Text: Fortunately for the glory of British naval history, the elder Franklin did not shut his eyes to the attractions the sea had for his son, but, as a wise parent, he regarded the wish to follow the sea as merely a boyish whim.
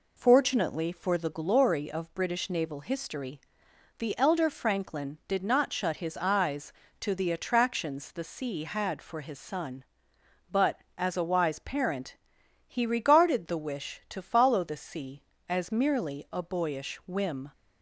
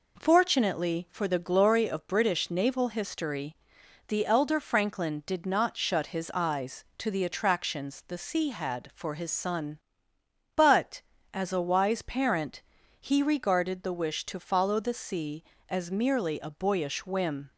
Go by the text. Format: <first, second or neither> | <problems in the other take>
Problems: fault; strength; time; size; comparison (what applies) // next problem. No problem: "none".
neither | none